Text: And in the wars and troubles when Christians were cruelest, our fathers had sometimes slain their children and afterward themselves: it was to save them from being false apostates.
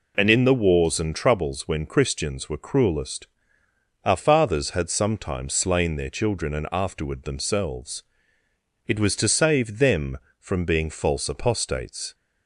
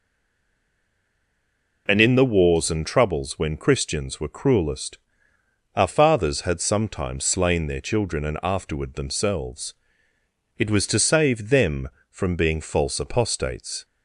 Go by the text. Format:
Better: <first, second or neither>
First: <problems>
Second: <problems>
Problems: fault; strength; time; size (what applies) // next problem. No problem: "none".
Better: first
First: none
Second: stays silent before the first word; noticeable; until 1.8 s; 1.8 s long